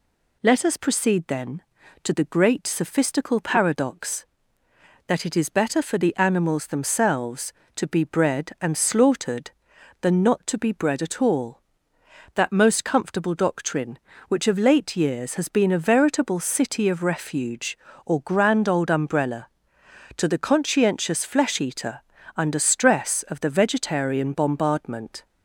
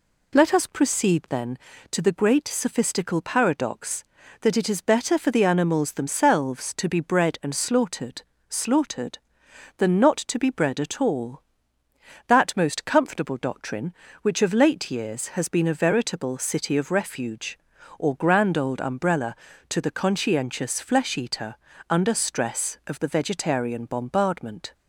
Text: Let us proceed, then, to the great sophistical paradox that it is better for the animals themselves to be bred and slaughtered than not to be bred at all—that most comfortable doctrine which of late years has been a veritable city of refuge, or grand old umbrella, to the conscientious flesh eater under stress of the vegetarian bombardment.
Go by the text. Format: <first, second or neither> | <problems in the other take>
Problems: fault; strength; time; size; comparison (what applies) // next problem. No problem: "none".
first | says "slaughtered" twice; at 8.4 s // pauses between "eater" and "under"; slight; at 21.5 s; 0.34 s long; slight in the first